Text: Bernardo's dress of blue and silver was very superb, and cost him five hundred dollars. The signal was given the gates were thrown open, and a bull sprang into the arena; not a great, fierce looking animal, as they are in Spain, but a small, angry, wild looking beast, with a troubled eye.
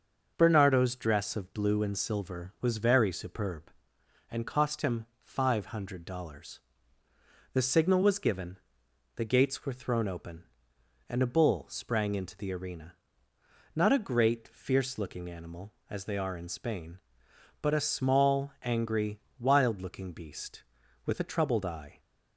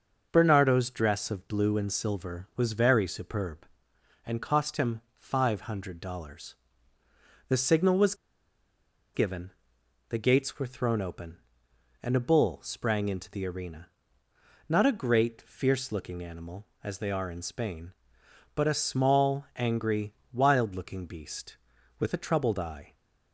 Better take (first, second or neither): first